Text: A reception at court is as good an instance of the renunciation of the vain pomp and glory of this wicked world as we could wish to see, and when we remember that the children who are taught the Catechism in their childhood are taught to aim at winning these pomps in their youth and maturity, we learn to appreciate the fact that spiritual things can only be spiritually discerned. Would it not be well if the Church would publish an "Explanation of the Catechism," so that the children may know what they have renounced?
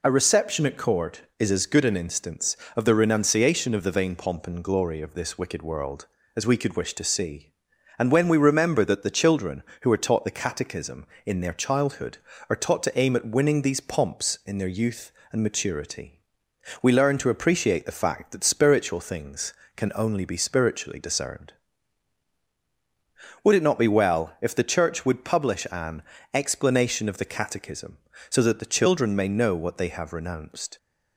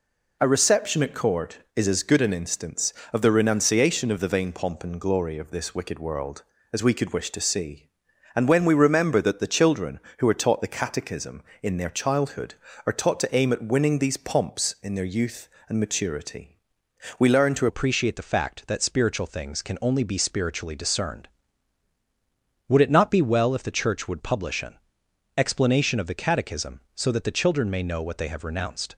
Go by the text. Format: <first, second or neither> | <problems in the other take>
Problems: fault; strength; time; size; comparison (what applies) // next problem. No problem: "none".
first | changes voice at "appreciate"; from 17.6 s on; 11.3 s long // pauses between "an" and "Explanation"; noticeable; at 24.7 s; 0.62 s long; slight in the first